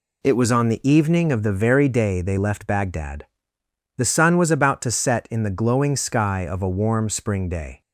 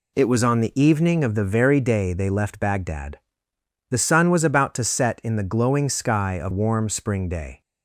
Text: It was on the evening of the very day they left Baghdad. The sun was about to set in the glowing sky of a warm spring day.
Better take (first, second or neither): first